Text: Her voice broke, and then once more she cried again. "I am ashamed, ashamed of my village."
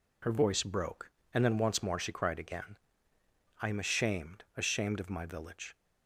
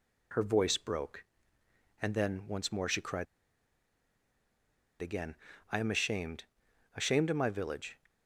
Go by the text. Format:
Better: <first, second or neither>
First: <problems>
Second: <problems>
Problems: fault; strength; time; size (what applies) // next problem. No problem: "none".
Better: first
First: none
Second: pauses between "cried" and "again"; strong; at 3.2 s; 1.7 s long